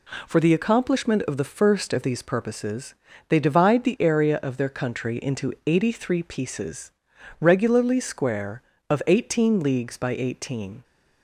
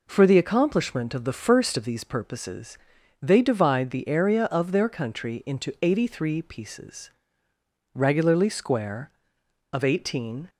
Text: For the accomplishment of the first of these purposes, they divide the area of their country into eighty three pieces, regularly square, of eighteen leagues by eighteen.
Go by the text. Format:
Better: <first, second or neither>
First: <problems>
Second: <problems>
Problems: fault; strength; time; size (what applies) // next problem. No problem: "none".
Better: first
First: none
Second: stops before "leagues by eighteen"; at 10.4 s